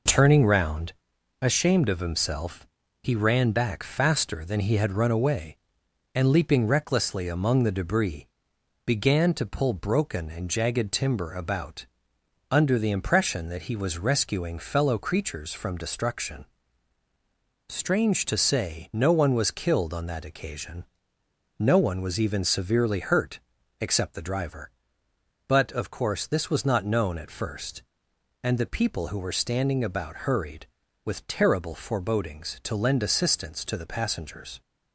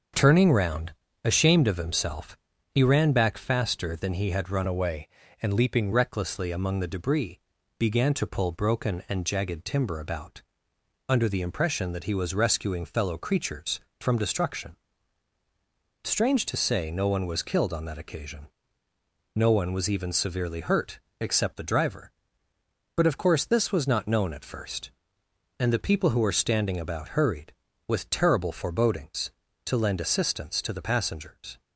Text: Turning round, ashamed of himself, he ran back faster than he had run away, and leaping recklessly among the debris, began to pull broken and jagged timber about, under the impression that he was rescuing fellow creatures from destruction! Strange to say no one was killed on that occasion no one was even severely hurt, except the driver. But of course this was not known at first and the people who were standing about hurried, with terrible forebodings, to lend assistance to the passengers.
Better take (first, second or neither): first